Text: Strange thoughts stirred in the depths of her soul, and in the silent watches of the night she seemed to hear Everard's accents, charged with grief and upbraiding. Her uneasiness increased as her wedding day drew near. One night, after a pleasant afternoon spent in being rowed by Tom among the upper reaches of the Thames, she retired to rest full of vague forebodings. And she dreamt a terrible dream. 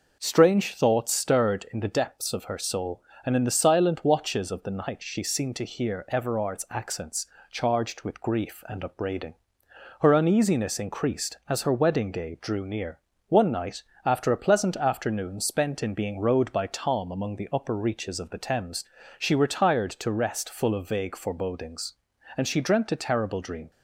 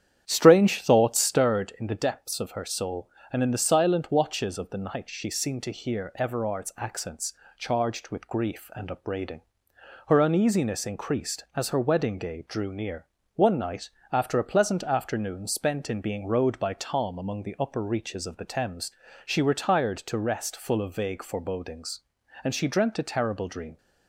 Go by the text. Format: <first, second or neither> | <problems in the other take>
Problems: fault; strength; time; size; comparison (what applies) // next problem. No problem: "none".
first | starts louder than the rest; strong; until 1.5 s; 9.5 dB